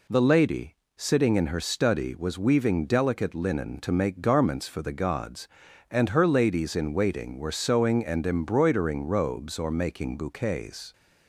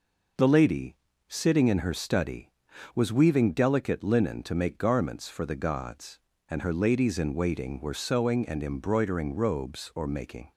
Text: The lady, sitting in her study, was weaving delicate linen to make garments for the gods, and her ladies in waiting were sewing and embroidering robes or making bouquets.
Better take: first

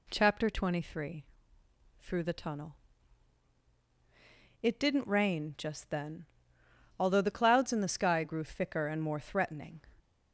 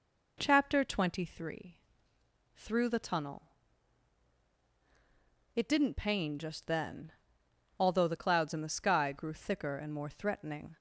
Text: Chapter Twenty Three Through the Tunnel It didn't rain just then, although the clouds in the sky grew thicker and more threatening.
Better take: first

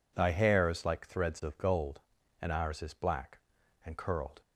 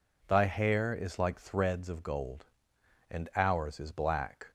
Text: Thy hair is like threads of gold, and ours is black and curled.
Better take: first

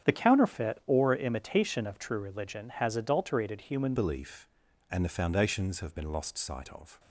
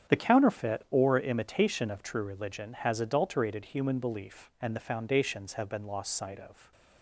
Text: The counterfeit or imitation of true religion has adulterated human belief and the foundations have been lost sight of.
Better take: second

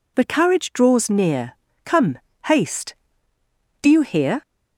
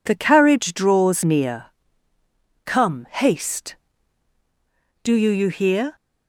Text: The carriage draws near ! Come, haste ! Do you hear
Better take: first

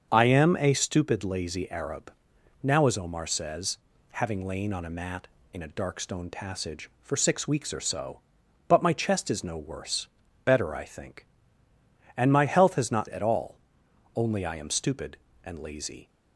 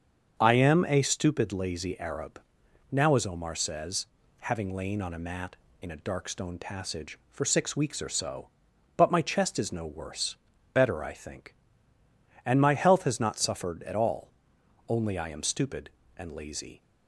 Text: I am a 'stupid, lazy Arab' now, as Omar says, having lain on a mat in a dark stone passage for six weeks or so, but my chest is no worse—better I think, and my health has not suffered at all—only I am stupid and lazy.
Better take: second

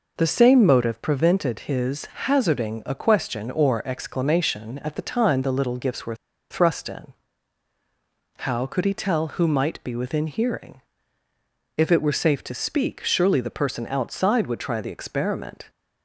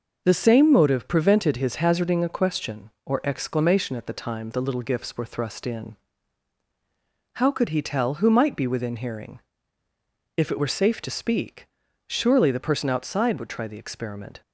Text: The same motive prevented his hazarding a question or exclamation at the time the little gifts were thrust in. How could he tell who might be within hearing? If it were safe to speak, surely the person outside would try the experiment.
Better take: second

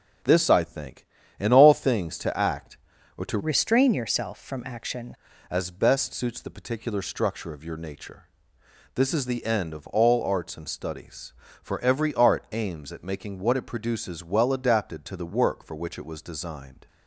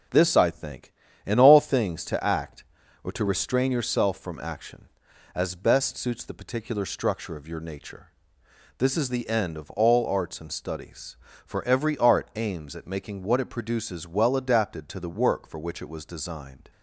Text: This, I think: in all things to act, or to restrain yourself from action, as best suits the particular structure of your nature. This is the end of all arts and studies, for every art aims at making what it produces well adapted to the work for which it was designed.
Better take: second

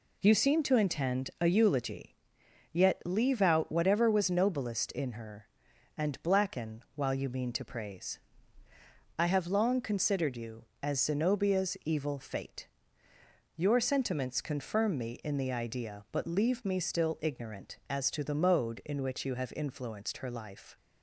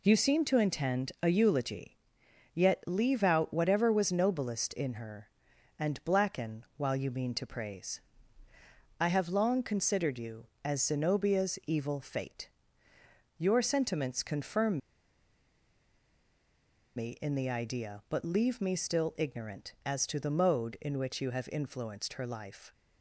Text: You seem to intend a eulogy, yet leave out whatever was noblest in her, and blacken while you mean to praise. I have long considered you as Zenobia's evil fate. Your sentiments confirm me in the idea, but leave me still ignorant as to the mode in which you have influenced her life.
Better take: first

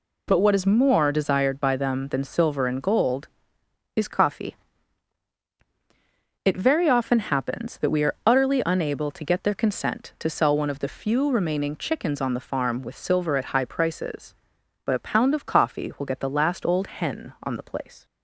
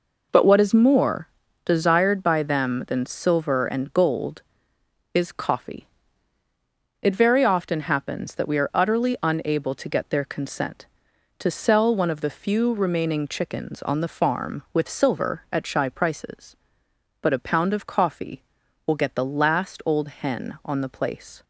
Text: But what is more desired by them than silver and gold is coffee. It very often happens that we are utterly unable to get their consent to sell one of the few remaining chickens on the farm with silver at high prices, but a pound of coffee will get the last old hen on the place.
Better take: first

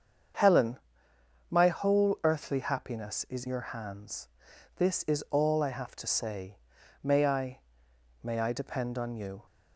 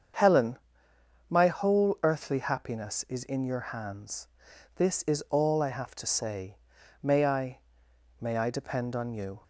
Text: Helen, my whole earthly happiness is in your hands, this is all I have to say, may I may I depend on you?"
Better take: second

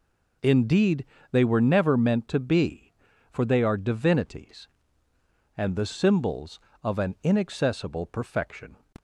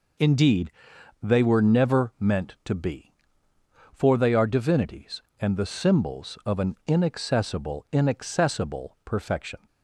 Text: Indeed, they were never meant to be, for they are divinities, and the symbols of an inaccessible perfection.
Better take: first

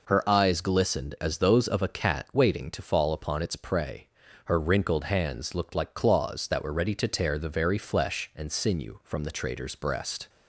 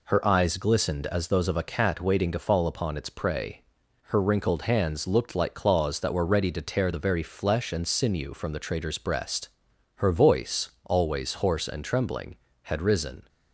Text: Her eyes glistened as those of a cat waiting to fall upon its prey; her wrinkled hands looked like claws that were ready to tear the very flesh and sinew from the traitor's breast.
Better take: first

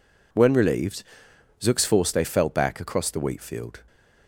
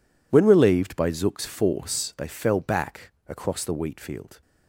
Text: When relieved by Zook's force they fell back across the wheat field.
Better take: second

